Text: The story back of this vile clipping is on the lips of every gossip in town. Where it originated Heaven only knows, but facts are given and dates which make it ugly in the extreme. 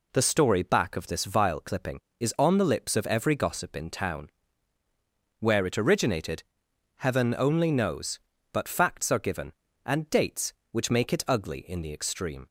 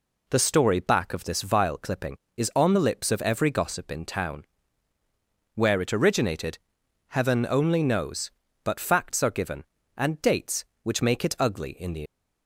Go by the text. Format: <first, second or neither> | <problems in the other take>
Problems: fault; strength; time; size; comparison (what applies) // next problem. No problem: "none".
first | pauses between "originated" and "Heaven"; noticeable; at 6.5 s; 0.52 s long; noticeable in the first // stops before "extreme"; at 12.0 s